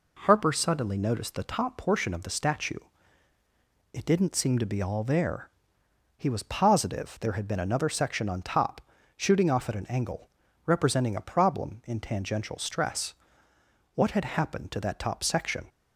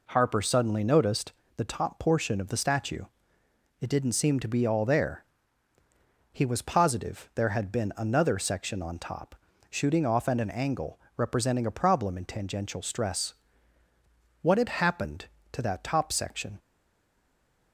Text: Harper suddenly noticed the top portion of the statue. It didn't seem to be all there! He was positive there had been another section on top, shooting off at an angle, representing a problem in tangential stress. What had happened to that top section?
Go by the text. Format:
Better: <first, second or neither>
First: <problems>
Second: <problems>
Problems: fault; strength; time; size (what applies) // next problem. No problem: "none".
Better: first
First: none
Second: pauses between "noticed" and "the"; slight; at 1.3 s; 0.24 s long // stays silent after the last word; from 16.5 s on; 1.2 s long